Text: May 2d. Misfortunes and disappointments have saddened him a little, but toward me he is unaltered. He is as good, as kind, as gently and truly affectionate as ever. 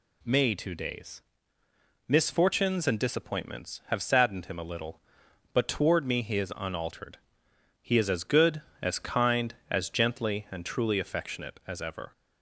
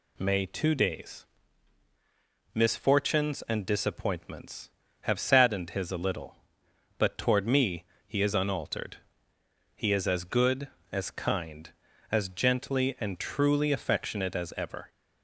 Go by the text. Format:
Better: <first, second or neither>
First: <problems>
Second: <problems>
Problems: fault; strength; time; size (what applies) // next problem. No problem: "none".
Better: first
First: none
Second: says "his" for "him"; at 5.7 s // pauses between "me" and "he"; slight; at 7.8 s; 0.22 s long